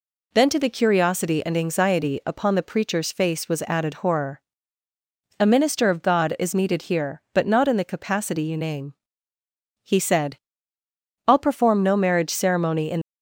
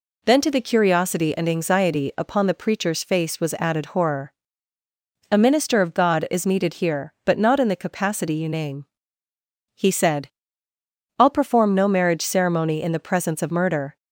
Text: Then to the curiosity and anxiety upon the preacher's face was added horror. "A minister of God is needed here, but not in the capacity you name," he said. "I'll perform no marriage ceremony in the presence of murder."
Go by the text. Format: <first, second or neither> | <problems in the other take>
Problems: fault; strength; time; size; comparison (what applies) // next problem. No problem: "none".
second | stops before "the presence of murder"; at 13.0 s